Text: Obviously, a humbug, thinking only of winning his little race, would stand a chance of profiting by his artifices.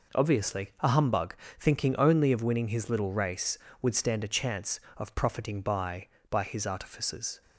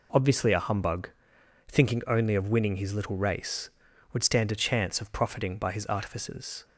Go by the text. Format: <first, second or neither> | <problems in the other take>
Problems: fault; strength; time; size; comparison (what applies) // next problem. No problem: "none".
second | says "by" twice; at 6.3 s